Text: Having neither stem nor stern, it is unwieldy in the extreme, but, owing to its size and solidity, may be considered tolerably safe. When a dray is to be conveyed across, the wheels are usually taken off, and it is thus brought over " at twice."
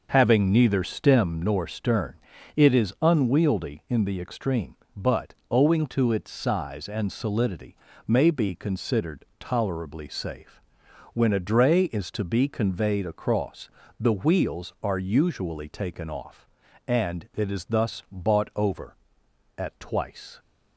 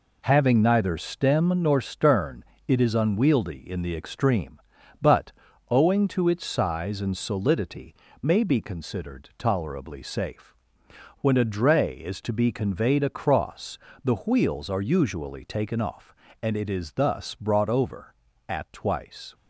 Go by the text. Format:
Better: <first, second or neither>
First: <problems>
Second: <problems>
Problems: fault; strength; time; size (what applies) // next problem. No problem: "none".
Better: second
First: starts louder than the rest; noticeable; until 1.1 s; 6 dB // says "bought" for "brought"; at 18.1 s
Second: none